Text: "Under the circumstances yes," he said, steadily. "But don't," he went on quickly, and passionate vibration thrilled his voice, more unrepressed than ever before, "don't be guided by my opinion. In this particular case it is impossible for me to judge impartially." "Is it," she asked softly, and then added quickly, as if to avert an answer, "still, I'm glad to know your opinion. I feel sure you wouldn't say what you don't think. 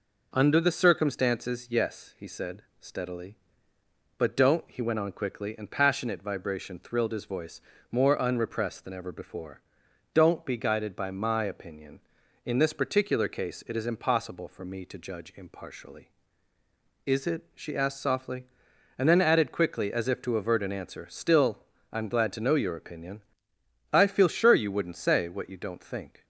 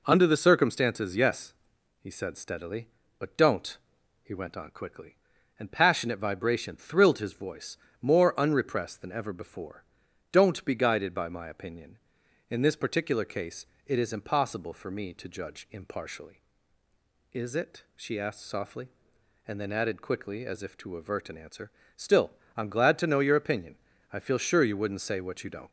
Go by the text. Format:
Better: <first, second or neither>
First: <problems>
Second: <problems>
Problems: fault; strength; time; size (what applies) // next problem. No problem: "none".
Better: first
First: none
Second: pauses between "case" and "it"; slight; at 13.6 s; 0.20 s long // stops before "think"; at 25.6 s